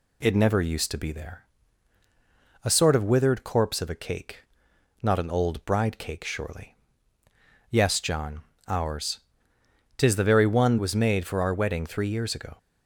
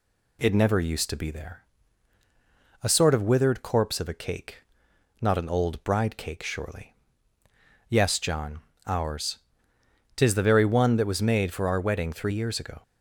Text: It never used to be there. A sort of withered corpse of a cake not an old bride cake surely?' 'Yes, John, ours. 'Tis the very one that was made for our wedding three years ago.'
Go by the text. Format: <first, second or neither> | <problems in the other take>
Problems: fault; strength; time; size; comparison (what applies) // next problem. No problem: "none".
second | pauses between "cake" and "not"; noticeable; at 4.4 s; 0.60 s long; noticeable in the second // skips "that"; at 10.7 s